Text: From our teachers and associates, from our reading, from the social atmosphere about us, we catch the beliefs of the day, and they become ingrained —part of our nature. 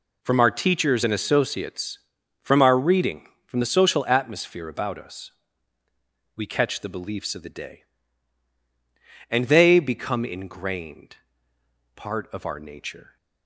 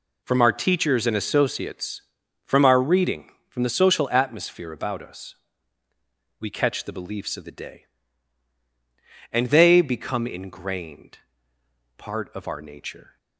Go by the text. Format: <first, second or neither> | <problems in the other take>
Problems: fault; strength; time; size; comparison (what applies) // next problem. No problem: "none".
neither | none